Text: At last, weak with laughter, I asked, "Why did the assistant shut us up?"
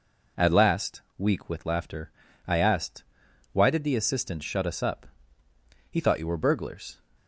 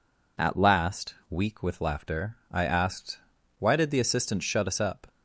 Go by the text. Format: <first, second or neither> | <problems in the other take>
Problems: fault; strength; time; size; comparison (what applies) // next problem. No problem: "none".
second | goes on to say "He thought you were burglars"; noticeable; from 5.9 s on; 1.0 s long